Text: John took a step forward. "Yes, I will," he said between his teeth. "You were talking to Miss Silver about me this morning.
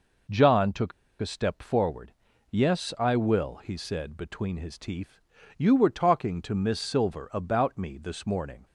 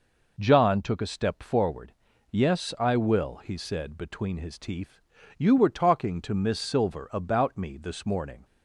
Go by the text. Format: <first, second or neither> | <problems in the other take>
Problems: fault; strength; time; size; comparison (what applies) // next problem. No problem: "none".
second | pauses between "took" and "a"; slight; at 0.9 s; 0.29 s long